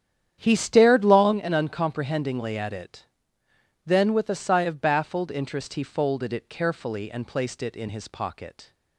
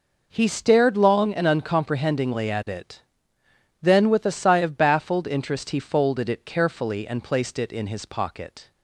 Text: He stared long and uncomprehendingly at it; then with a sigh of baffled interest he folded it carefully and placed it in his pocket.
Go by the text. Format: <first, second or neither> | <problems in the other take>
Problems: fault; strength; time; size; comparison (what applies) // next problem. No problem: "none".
second | starts louder than the rest; strong; until 1.4 s; 9.5 dB